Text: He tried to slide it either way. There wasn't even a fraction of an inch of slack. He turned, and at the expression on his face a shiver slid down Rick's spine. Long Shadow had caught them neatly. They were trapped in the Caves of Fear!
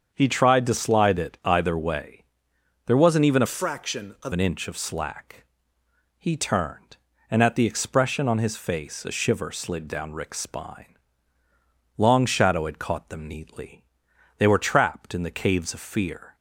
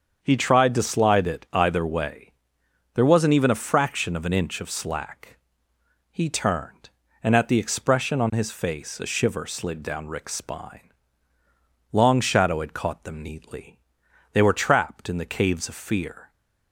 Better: second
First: starts louder than the rest; until 1.1 s; 7 dB // changes voice from "fraction" to "of"; from 3.4 to 4.3 s; 0.9 s long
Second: starts louder than the rest; until 1.2 s; 7 dB

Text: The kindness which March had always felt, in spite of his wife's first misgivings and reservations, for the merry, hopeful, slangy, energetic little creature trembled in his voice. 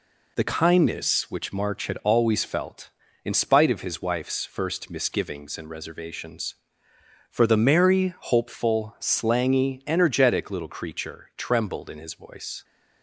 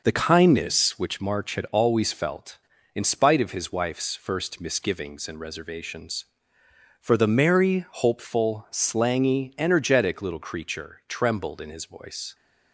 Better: first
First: none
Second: starts louder than the rest; noticeable; until 1.1 s; 5.5 dB

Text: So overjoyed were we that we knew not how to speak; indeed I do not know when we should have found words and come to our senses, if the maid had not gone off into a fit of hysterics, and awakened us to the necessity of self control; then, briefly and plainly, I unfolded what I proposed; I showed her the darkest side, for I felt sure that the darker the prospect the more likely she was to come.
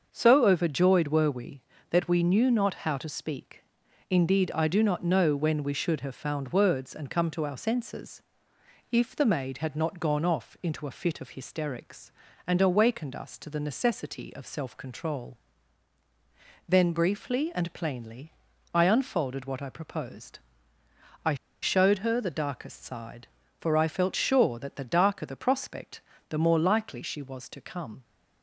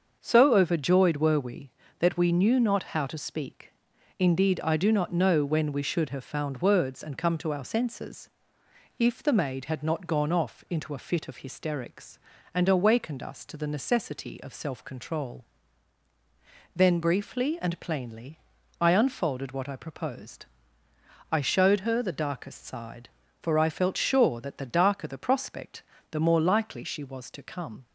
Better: second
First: starts louder than the rest; until 1.1 s; 6.5 dB // pauses between "I" and "showed"; slight; at 21.3 s; 0.26 s long // pauses between "prospect" and "the"; slight; at 26.0 s; 0.28 s long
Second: starts louder than the rest; until 1.2 s; 6.5 dB // pauses between "prospect" and "the"; slight; at 25.8 s; 0.28 s long

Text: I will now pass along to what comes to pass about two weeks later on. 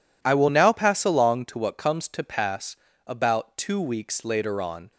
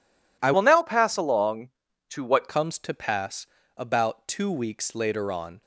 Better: first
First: pauses between "pass" and "about"; slight; at 2.7 s; 0.32 s long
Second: changes voice from "will" to "what"; from 0.5 to 2.4 s; 1.9 s long // pauses between "pass" and "about"; slight; at 3.4 s; 0.32 s long

